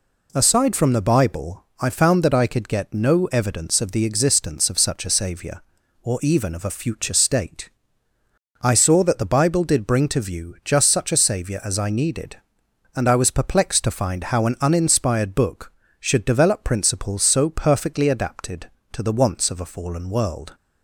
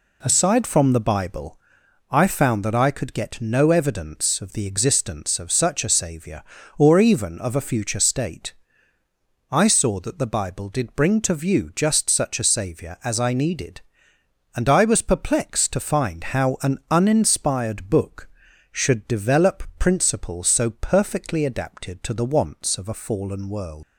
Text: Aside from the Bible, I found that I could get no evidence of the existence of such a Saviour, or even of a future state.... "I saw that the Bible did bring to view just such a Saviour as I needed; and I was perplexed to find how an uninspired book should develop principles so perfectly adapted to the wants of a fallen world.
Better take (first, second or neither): first